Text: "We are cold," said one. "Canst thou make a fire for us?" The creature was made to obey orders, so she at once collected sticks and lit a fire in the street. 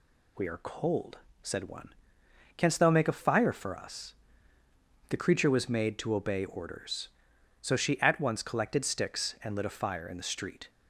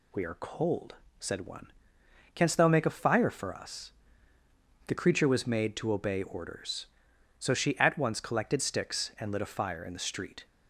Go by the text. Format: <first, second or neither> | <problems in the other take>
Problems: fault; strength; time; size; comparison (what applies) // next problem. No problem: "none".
neither | none